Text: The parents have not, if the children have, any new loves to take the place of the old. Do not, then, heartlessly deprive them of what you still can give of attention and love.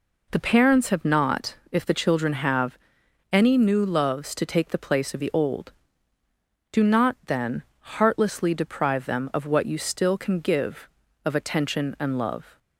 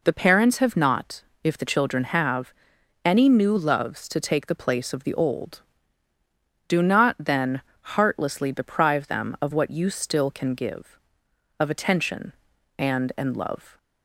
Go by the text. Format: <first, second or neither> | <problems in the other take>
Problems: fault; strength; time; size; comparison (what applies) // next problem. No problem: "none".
first | says "and" twice; at 13.1 s